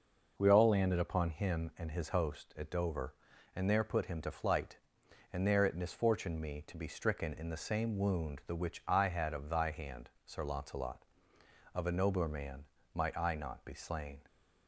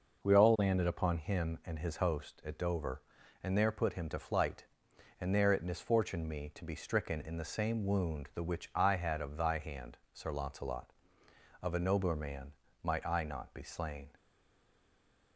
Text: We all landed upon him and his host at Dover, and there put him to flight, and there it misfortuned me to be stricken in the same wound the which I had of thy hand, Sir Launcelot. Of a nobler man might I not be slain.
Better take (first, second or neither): first